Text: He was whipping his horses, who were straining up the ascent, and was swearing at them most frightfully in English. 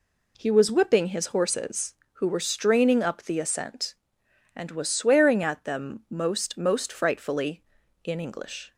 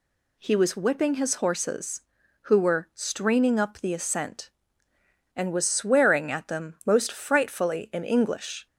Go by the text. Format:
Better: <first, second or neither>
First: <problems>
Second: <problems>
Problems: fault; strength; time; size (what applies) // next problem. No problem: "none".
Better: second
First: says "most" twice; at 6.5 s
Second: none